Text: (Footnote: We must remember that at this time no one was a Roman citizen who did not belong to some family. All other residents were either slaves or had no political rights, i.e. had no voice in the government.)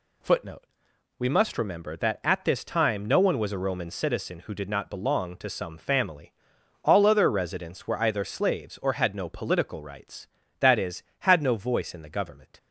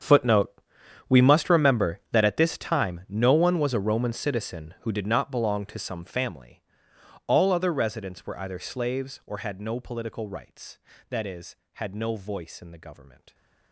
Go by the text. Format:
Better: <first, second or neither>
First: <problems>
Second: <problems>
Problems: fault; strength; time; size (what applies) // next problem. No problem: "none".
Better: first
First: none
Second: gets quieter; strong; throughout; 18 dB